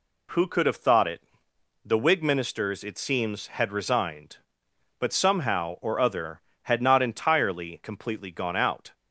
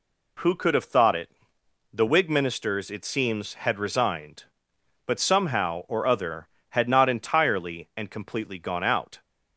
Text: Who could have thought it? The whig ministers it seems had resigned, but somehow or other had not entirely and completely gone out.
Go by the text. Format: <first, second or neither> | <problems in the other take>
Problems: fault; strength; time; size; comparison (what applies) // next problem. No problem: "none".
second | skips "and"; at 7.8 s